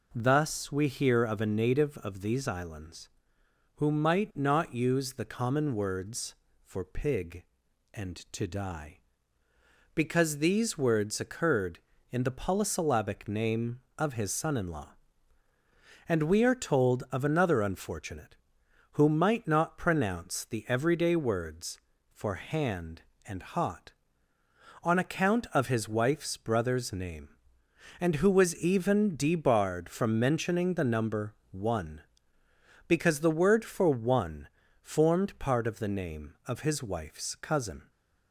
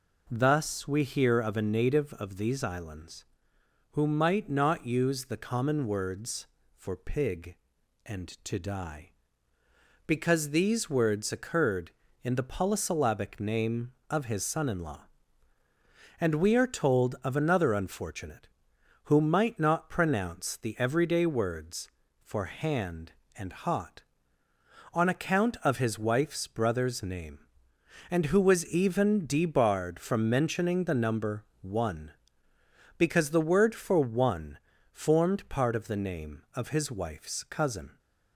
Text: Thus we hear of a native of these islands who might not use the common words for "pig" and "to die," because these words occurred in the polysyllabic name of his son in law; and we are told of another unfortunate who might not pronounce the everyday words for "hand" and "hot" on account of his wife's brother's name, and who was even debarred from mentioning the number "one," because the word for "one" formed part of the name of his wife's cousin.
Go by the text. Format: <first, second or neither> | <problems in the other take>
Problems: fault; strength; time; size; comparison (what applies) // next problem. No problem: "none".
neither | pauses between "number" and "one"; slight; the same in both // pauses between "one" and "formed"; slight; the same in both